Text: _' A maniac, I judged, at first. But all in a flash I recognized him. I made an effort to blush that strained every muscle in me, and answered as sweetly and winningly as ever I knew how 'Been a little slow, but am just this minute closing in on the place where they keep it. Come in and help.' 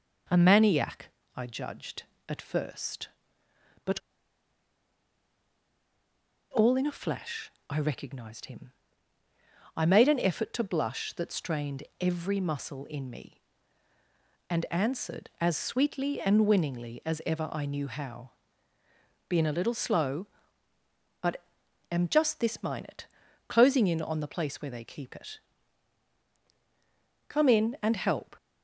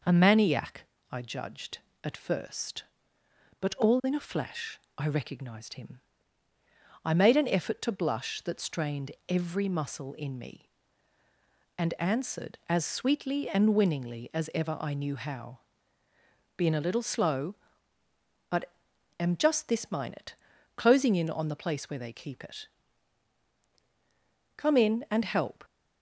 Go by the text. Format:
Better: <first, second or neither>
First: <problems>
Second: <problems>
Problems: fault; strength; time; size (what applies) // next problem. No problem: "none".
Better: second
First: pauses between "But" and "all"; strong; at 3.9 s; 2.5 s long // pauses between "flash" and "I"; slight; at 7.5 s; 0.18 s long // pauses between "strained" and "every"; slight; at 11.8 s; 0.18 s long // pauses between "how" and "Been"; noticeable; at 18.3 s; 0.98 s long // pauses between "but" and "am"; noticeable; at 21.4 s; 0.48 s long // pauses between "minute" and "closing"; at 23.0 s; 0.40 s long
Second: pauses between "flash" and "I"; slight; at 4.7 s; 0.18 s long // pauses between "strained" and "every"; slight; at 9.1 s; 0.18 s long // pauses between "how" and "Been"; noticeable; at 15.5 s; 0.98 s long // pauses between "but" and "am"; noticeable; at 18.7 s; 0.48 s long // pauses between "minute" and "closing"; at 20.3 s; 0.40 s long